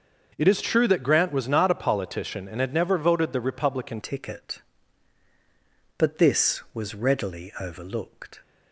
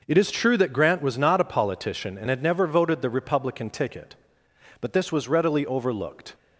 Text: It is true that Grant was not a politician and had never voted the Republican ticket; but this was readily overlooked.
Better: second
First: starts louder than the rest; until 1.3 s; 6 dB // changes voice at "ticket"; from 4.0 s on; 4.4 s long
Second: none

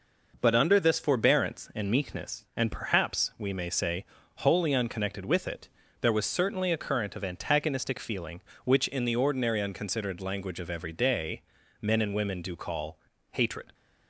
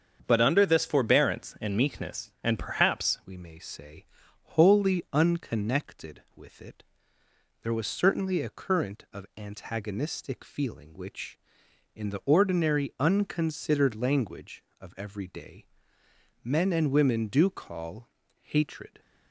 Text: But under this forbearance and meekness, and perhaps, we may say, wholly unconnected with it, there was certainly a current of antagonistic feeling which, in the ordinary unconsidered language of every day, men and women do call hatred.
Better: first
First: pauses between "call" and "hatred"; slight; at 12.9 s; 0.34 s long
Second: starts louder than the rest; strong; until 1.2 s; 7 dB // changes voice at "we"; from 3.2 s on; 15.7 s long // pauses between "call" and "hatred"; slight; at 18.0 s; 0.34 s long

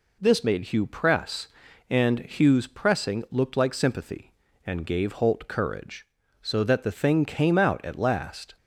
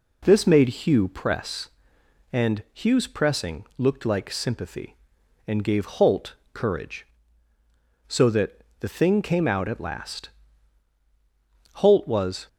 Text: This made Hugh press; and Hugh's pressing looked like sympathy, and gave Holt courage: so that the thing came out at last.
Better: first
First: none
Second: pauses between "Holt" and "courage"; slight; at 6.3 s; 0.18 s long // pauses between "that" and "the"; slight; at 8.6 s; 0.16 s long // goes on to say "Holt was"; noticeable; from 11.7 s on; 0.74 s long

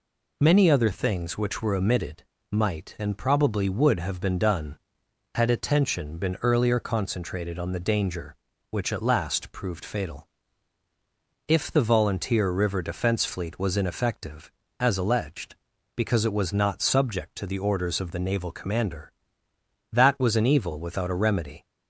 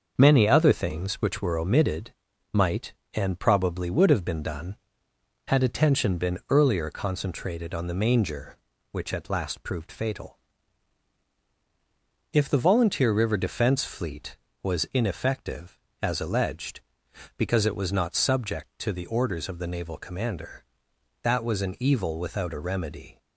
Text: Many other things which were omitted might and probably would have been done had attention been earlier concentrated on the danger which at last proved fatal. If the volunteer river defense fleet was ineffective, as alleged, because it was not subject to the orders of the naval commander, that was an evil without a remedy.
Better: first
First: pauses between "omitted" and "might"; slight; at 2.2 s; 0.30 s long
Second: starts louder than the rest; until 1.1 s; 6.5 dB // pauses between "omitted" and "might"; at 2.1 s; 0.40 s long // says "manger" for "danger"; at 7.9 s

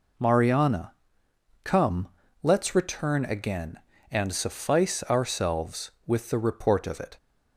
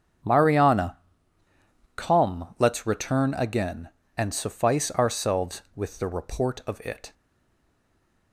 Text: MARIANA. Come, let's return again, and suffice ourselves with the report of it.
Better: first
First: none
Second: starts louder than the rest; strong; until 2.2 s; 8 dB // stays silent after the last word; noticeable; from 7.1 s on; 1.2 s long

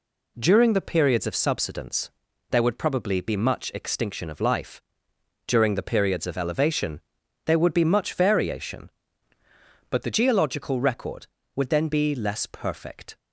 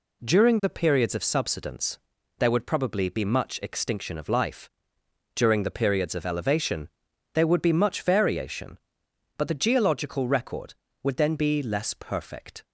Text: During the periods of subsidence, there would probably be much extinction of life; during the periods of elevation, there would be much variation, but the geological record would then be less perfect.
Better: second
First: changes voice from "but" to "the"; from 9.8 to 10.0 s; 0.2 s long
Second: none

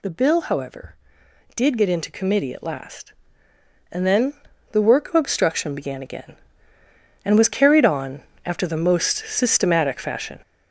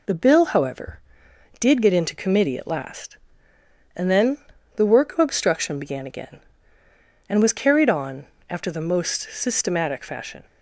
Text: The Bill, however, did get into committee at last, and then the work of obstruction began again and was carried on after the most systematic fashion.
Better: second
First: gets louder; throughout; 6.5 dB // pauses between "then" and "the"; at 4.3 s; 0.38 s long // pauses between "on" and "after"; slight; at 8.2 s; 0.24 s long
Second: pauses between "then" and "the"; at 4.3 s; 0.38 s long // pauses between "on" and "after"; slight; at 8.2 s; 0.24 s long

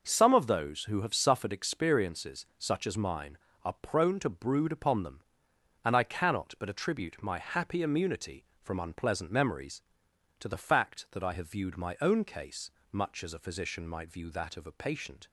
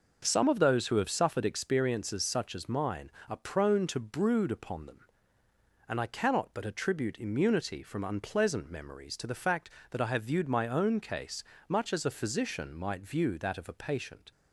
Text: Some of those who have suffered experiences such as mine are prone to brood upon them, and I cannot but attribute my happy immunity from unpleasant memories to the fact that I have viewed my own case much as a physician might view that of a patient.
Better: first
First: pauses between "case" and "much"; slight; at 12.7 s; 0.22 s long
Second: skips "my happy"; at 7.1 s // pauses between "case" and "much"; slight; at 11.4 s; 0.24 s long

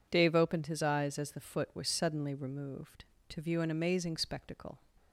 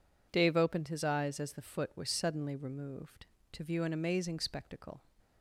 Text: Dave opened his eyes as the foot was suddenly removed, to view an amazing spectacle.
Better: neither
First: none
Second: none

